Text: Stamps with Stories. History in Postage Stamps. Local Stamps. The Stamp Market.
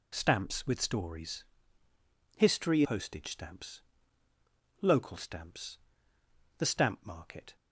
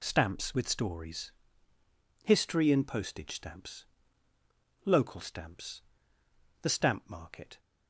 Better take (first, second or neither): second